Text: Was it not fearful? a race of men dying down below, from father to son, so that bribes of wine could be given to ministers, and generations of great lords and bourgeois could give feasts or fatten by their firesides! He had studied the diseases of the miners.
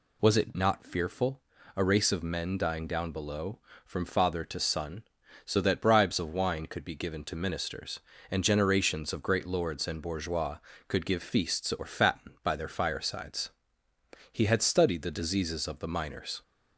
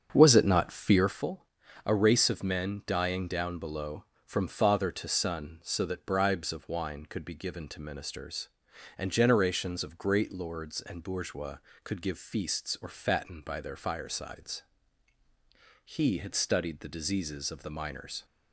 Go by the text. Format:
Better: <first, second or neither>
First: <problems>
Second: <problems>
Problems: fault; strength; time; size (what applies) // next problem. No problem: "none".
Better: first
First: none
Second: starts louder than the rest; strong; until 1.3 s; 7.5 dB